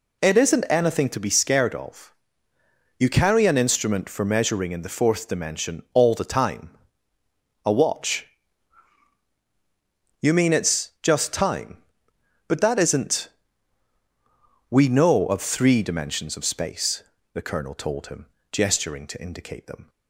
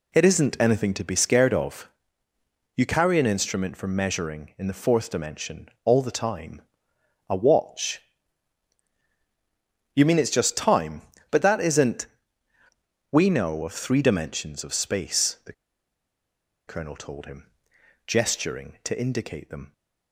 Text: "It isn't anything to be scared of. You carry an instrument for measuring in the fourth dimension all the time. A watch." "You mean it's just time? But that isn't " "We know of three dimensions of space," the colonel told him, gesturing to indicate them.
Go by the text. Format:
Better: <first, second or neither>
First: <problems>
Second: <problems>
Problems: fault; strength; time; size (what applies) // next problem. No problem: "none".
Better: first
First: none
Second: pauses between "the" and "colonel"; at 15.5 s; 1.1 s long